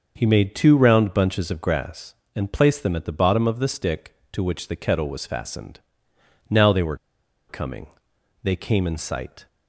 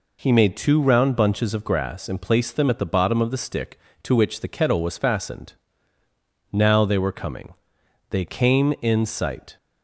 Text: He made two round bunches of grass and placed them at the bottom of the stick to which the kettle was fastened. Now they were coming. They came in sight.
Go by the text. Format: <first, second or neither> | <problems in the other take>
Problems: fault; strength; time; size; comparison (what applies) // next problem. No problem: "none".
second | starts louder than the rest; noticeable; until 1.1 s; 6 dB // pauses between "were" and "coming"; noticeable; at 6.9 s; 0.52 s long